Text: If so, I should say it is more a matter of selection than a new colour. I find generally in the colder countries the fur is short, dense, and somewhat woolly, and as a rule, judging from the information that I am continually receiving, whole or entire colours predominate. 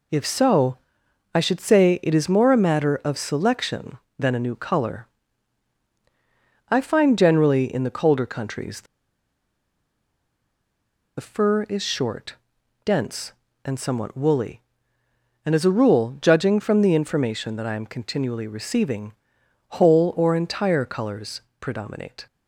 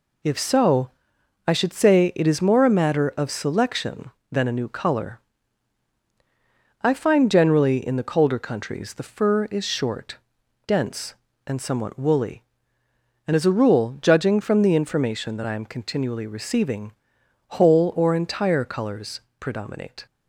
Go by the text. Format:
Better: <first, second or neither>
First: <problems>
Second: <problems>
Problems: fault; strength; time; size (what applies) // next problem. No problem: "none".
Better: second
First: pauses between "the" and "fur"; strong; at 8.8 s; 2.3 s long // pauses between "colours" and "predominate"; slight; at 21.4 s; 0.20 s long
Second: pauses between "colours" and "predominate"; slight; at 19.1 s; 0.20 s long